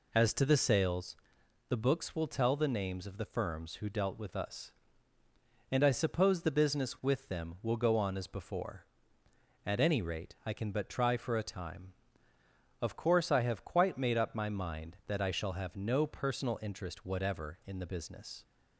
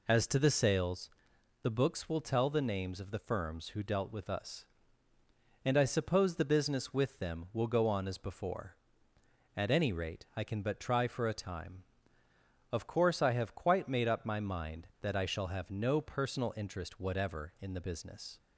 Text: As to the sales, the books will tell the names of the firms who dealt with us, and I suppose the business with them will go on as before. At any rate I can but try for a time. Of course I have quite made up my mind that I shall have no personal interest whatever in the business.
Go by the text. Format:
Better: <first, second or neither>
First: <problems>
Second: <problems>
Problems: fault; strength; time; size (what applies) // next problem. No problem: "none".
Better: neither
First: none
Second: none